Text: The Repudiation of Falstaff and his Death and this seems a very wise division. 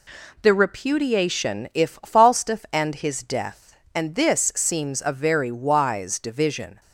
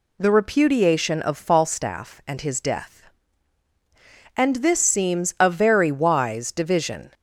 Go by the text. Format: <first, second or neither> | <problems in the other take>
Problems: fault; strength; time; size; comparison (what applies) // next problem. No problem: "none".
second | says "if" for "of"; at 1.7 s